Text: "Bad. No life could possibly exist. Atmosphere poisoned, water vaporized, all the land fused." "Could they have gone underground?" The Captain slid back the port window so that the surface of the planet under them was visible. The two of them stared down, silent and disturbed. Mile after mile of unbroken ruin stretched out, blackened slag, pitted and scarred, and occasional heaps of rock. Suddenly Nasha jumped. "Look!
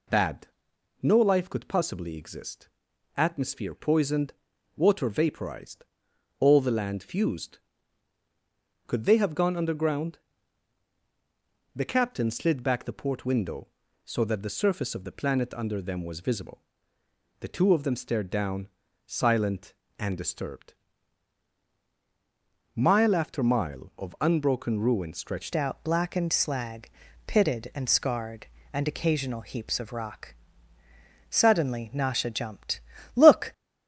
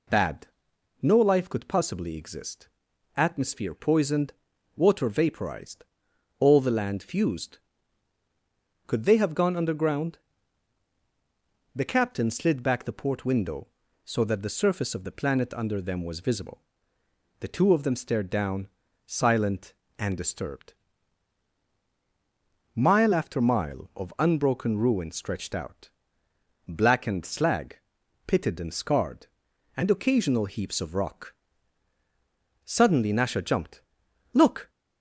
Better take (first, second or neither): second